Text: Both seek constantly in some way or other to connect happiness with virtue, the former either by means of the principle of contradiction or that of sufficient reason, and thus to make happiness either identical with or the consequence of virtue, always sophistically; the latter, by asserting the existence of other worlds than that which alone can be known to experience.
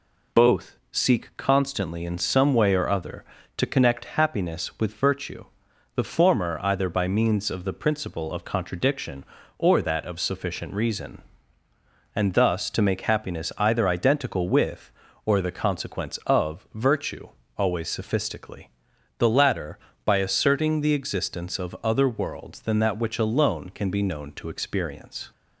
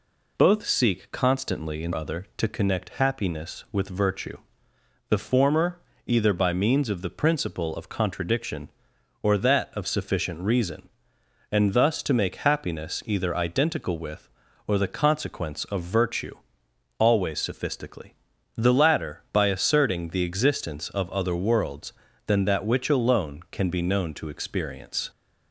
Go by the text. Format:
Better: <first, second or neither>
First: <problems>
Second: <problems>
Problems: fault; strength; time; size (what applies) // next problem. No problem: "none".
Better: first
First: none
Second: skips "some way or"; at 1.9 s // pauses between "former" and "either"; slight; at 5.7 s; 0.26 s long